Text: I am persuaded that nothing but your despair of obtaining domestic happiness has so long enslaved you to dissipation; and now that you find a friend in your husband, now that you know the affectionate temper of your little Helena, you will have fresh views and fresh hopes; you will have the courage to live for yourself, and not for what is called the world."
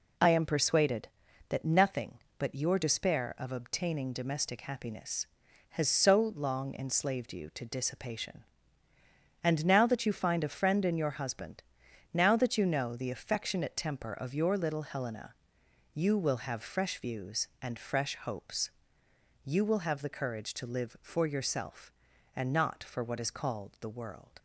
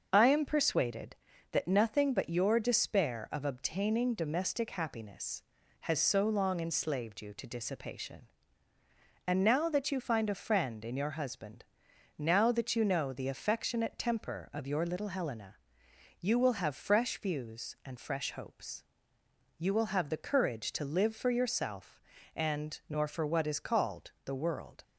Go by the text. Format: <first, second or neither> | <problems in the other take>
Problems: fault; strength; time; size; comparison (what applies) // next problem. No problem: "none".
first | starts louder than the rest; until 1.1 s; 6.5 dB // says "nor" for "not"; at 22.8 s